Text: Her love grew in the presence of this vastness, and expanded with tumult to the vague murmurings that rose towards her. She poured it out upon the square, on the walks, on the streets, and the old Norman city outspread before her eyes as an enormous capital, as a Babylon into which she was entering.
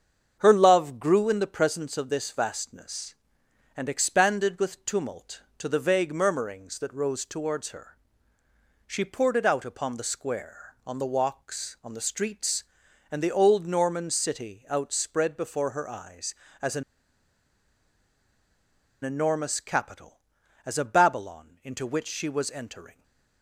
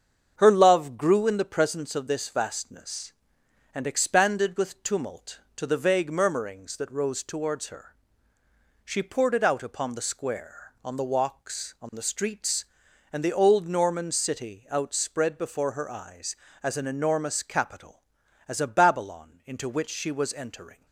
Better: second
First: starts louder than the rest; strong; until 1.4 s; 7 dB // pauses between "an" and "enormous"; strong; at 16.8 s; 2.2 s long // stays silent after the last word; slight; from 22.9 s on; 0.5 s long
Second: starts louder than the rest; strong; until 1.3 s; 7 dB

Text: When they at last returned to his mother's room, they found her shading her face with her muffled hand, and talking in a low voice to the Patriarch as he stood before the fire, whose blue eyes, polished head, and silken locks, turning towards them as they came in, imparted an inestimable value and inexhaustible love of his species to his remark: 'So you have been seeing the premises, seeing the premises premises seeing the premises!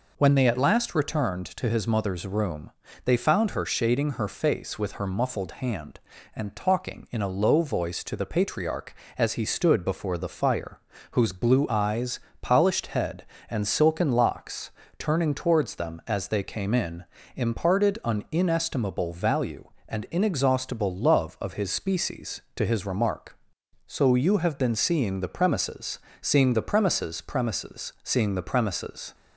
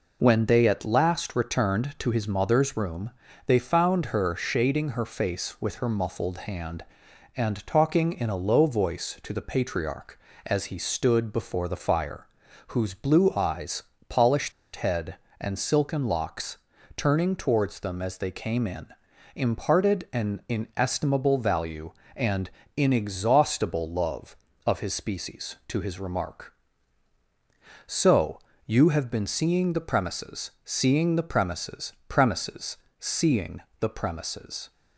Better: first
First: none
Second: pauses between "polished" and "head"; slight; at 14.5 s; 0.23 s long // pauses between "and" and "inexhaustible"; slight; at 22.4 s; 0.26 s long // pauses between "So" and "you"; slight; at 28.3 s; 0.24 s long // pauses between "premises" and "premises"; slight; at 31.9 s; 0.16 s long // pauses between "premises" and "seeing"; slight; at 32.7 s; 0.24 s long // pauses between "seeing" and "the"; slight; at 33.5 s; 0.20 s long

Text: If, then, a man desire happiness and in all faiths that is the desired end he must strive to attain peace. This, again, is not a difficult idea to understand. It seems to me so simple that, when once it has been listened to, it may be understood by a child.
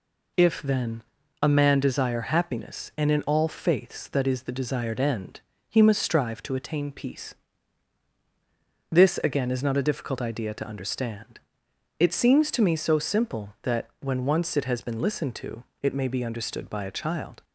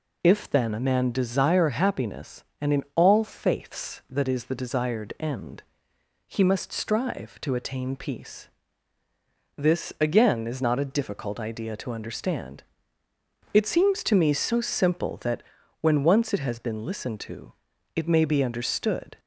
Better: first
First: pauses between "end" and "he"; slight; at 5.4 s; 0.26 s long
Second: pauses between "end" and "he"; noticeable; at 5.6 s; 0.68 s long // stops before "by a child"; at 19.1 s

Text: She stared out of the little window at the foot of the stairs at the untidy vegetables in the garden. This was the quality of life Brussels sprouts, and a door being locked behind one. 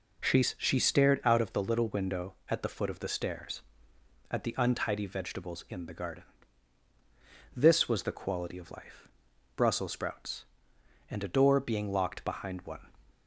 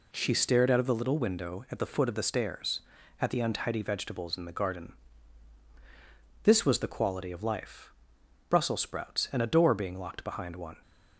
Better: second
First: says "She" twice; at 0.4 s // pauses between "life" and "Brussels"; noticeable; at 9.0 s; 0.48 s long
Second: pauses between "life" and "Brussels"; noticeable; at 7.9 s; 0.56 s long

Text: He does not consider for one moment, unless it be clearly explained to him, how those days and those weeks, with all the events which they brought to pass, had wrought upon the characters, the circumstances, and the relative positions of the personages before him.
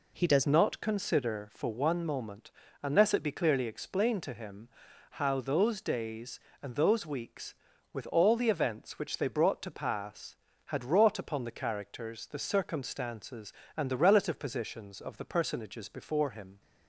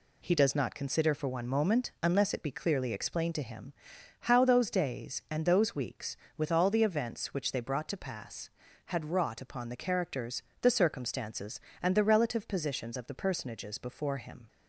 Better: second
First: changes voice at "not"; from 0.4 s on; 16.2 s long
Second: none

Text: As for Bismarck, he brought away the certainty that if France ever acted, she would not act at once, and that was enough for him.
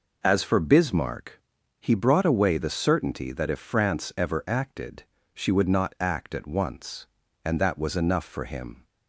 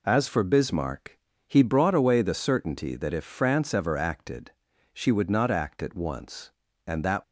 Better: first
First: none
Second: stops before "was enough for him"; at 7.2 s

